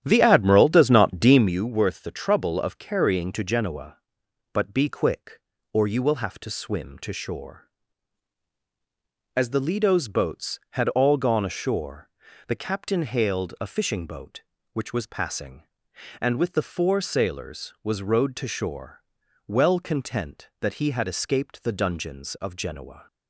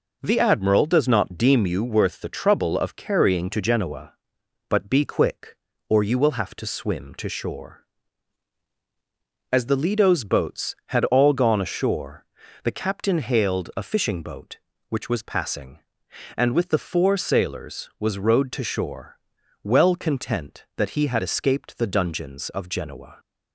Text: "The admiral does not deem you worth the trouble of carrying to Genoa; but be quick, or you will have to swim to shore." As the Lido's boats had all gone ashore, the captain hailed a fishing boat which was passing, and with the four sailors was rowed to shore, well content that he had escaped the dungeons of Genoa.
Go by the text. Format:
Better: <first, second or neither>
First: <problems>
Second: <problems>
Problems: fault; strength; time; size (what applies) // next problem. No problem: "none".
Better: second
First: starts louder than the rest; strong; until 1.6 s; 10.5 dB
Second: none